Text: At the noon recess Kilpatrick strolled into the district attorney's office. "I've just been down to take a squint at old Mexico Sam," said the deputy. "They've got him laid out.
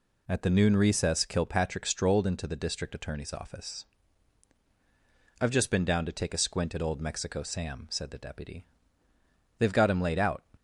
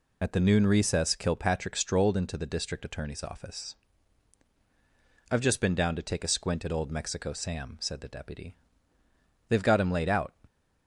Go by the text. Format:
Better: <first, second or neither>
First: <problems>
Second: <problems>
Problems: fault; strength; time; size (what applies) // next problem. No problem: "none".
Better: first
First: none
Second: loses the start of "At"; at 0.2 s; 40 ms